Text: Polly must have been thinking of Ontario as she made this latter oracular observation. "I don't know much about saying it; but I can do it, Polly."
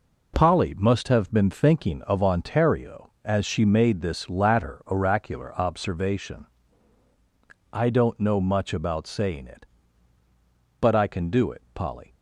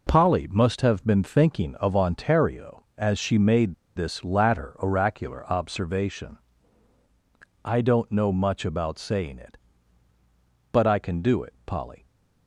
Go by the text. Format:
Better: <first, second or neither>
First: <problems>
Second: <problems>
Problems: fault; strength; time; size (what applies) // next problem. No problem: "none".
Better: first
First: none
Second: pauses between "made" and "this"; slight; at 3.7 s; 0.22 s long